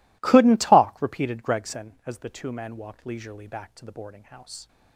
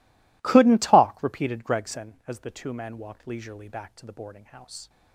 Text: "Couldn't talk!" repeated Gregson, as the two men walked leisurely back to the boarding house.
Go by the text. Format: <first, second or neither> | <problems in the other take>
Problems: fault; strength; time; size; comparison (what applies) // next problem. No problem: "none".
neither | none